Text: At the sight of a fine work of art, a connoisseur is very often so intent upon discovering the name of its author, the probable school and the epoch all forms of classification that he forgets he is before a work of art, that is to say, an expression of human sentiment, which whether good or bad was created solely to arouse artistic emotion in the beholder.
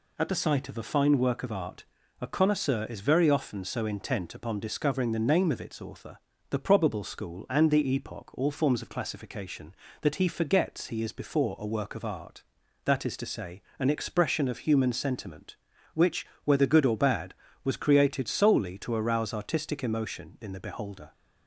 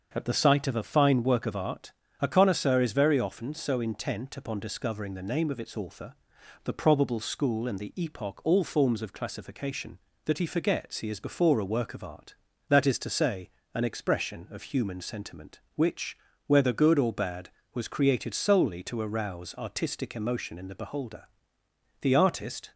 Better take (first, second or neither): first